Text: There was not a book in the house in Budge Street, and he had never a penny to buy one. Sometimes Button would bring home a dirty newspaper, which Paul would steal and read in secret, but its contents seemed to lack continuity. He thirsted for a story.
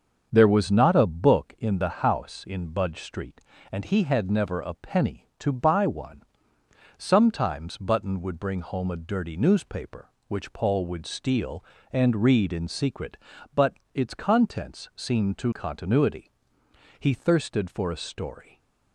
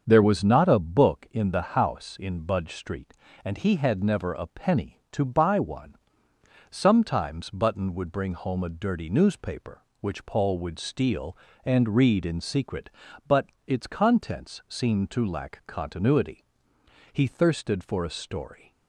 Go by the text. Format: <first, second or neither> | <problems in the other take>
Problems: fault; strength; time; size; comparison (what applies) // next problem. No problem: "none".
second | starts louder than the rest; until 1.3 s; 7 dB; also in the second // pauses between "but" and "its"; slight; at 13.7 s; 0.20 s long; slight in the second // skips "lack"; at 15.5 s // stays silent after the last word; slight; from 18.4 s on; 0.5 s long